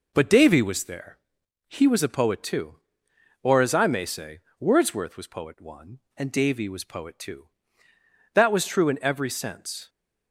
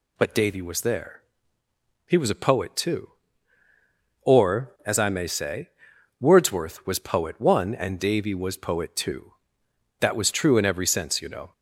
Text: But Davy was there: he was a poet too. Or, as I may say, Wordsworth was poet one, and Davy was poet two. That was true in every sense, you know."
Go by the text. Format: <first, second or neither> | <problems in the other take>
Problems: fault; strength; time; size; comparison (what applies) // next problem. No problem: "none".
second | stops before "you know"; at 9.8 s